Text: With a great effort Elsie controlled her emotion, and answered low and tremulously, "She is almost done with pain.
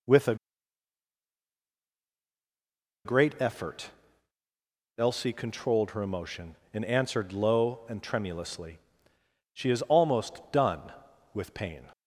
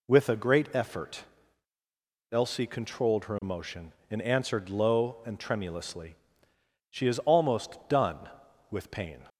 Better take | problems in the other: second | pauses between "a" and "great"; strong; at 0.3 s; 2.6 s long // pauses between "effort" and "Elsie"; at 3.9 s; 1.0 s long; also in the second

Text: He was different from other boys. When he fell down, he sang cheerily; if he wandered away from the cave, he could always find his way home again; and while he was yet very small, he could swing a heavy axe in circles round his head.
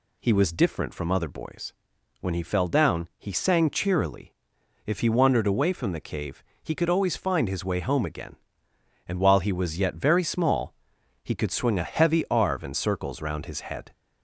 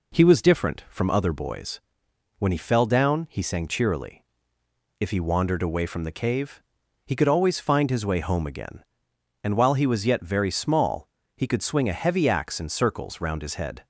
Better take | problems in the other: second | says "arve" for "axe"; at 12.2 s

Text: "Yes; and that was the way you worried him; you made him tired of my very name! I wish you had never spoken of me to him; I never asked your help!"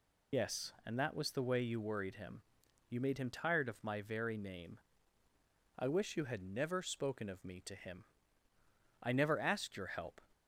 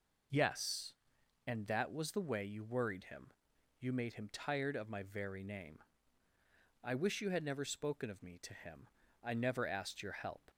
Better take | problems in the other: second | loses the start of "Yes"; at 0.3 s; 60 ms

